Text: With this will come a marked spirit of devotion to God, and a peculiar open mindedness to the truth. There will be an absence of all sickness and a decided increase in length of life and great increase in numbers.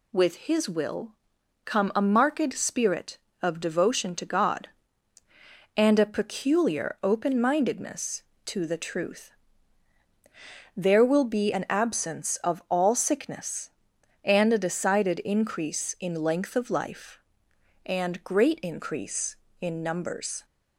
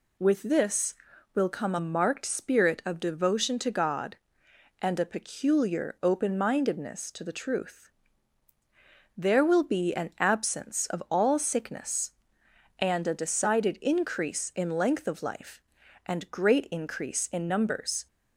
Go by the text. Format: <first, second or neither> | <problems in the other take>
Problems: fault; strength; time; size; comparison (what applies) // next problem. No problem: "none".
second | says "his" for "this"; at 0.3 s // pauses between "will" and "come"; noticeable; at 1.1 s; 0.52 s long